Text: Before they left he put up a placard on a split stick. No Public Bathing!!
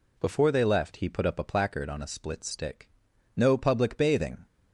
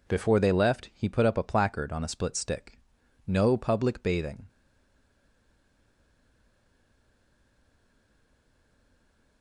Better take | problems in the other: first | stays silent after the last word; strong; from 4.4 s on; 5.0 s long

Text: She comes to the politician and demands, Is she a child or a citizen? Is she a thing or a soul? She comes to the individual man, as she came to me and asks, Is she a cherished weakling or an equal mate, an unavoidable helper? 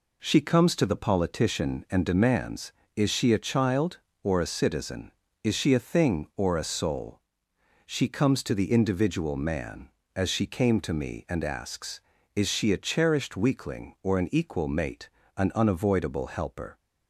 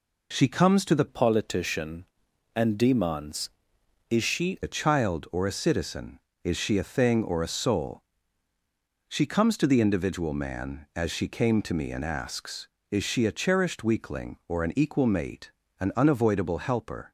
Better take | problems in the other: first | changes voice from "politician" to "she"; from 1.0 to 4.5 s; 3.5 s long

